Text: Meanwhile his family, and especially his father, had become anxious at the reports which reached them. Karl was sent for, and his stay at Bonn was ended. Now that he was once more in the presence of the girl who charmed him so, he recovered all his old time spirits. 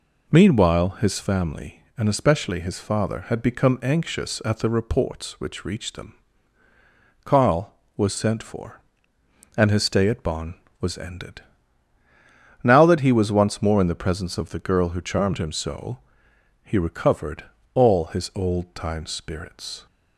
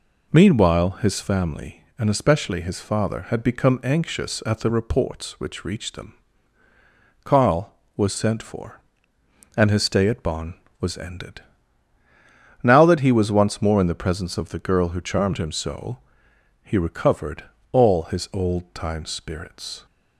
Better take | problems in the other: neither | pauses between "recovered" and "all"; slight; the same in both

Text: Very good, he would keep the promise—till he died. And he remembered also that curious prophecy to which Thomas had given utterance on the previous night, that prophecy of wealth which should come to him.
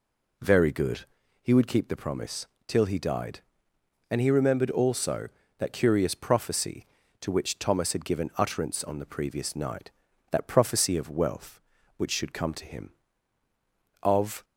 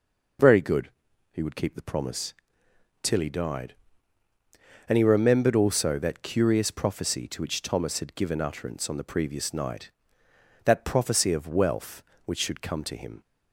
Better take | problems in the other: second | goes on to say "Of"; slight; from 14.0 s on; 0.42 s long

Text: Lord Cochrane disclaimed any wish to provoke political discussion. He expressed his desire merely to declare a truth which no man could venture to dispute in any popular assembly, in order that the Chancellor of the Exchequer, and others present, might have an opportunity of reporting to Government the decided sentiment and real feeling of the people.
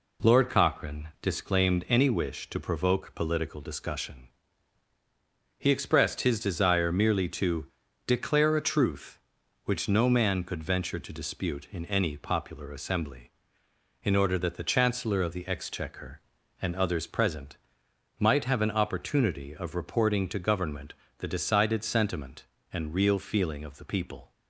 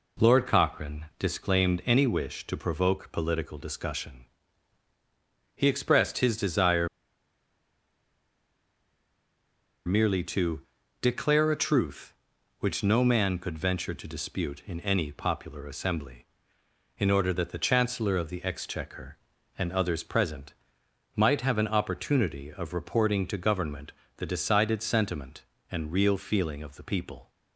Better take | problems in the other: first | pauses between "Cochrane" and "disclaimed"; slight; at 1.0 s; 0.16 s long; slight in the first // pauses between "desire" and "merely"; strong; at 6.8 s; 2.9 s long // pauses between "to" and "declare"; at 10.5 s; 0.40 s long; also in the first // pauses between "Government" and "the"; slight; at 23.9 s; 0.26 s long; slight in the first

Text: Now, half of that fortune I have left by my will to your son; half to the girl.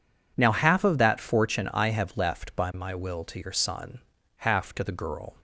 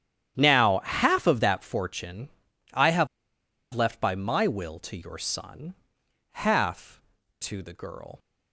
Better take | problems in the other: first | starts louder than the rest; strong; until 1.3 s; 10.5 dB // pauses between "fortune" and "I"; noticeable; at 2.2 s; 0.46 s long // pauses between "have" and "left"; noticeable; at 3.0 s; 0.67 s long

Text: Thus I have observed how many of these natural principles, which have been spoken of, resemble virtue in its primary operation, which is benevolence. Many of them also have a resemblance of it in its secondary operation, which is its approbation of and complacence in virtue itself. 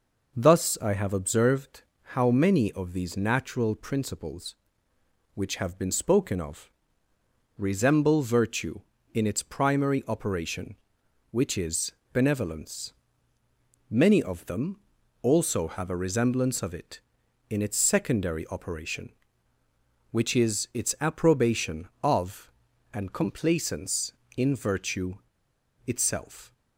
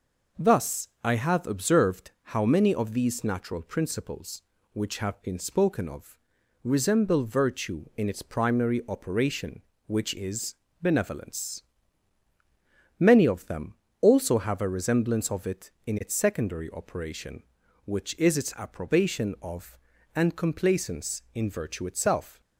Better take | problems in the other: second | pauses between "observed" and "how"; slight; at 1.8 s; 0.32 s long; slight in the second // pauses between "is" and "benevolence"; slight; at 11.9 s; 0.20 s long; slight in the second // pauses between "them" and "also"; at 14.7 s; 0.44 s long; slight in the second // pauses between "virtue" and "itself"; noticeable; at 25.1 s; 0.72 s long

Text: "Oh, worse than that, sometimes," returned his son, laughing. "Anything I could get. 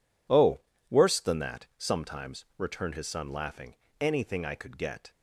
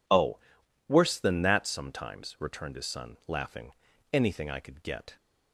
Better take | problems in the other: neither | none

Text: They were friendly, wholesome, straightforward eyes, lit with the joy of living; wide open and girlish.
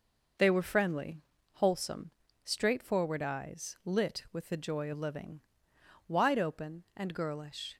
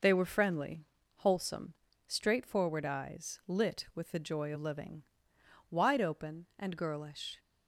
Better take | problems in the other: neither | none

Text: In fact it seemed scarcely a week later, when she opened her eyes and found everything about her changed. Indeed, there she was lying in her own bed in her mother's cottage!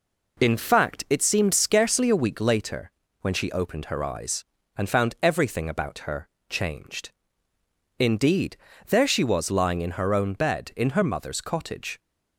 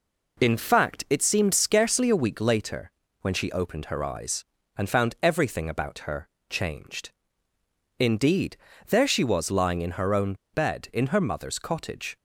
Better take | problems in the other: first | pauses between "her" and "changed"; slight; at 6.2 s; 0.20 s long; slight in the first // pauses between "own" and "bed"; slight; at 10.3 s; 0.18 s long

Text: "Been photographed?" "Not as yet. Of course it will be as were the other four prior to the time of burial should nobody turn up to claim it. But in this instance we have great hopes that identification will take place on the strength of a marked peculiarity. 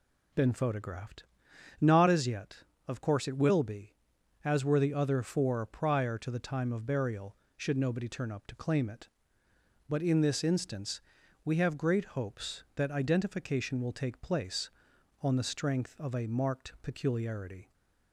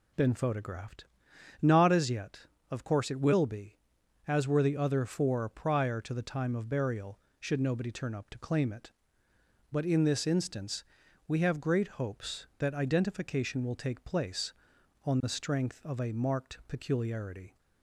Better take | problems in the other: neither | pauses between "instance" and "we"; the same in both

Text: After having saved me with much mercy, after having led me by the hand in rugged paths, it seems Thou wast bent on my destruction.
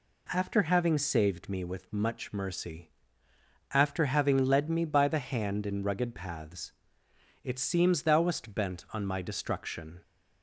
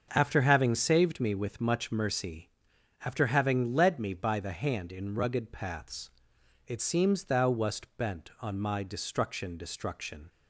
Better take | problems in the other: first | starts louder than the rest; until 1.1 s; 6.5 dB // says "destruction" twice; at 9.5 s

